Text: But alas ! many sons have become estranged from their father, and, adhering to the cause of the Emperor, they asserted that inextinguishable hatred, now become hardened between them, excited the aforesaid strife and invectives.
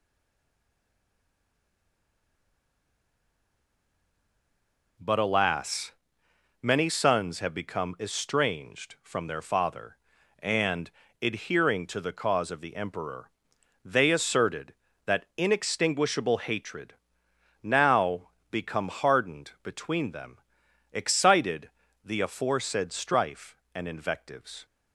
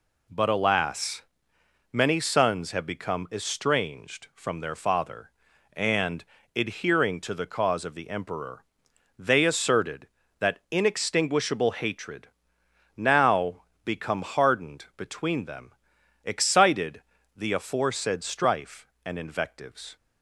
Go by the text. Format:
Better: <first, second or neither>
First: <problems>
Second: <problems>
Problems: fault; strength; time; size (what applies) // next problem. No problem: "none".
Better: second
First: stays silent before the first word; strong; until 4.9 s; 4.9 s long // pauses between "now" and "become"; slight; at 18.2 s; 0.22 s long // pauses between "excited" and "the"; slight; at 21.6 s; 0.34 s long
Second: pauses between "now" and "become"; slight; at 13.6 s; 0.22 s long // pauses between "excited" and "the"; slight; at 17.0 s; 0.34 s long